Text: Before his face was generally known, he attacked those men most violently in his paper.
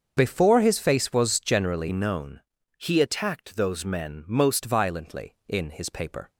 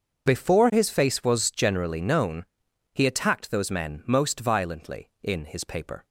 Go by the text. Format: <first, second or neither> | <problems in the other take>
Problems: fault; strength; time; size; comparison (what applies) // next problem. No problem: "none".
second | starts louder than the rest; until 1.1 s; 6.5 dB; also in the second // changes voice from "known" to "most"; from 1.9 to 4.6 s; 2.7 s long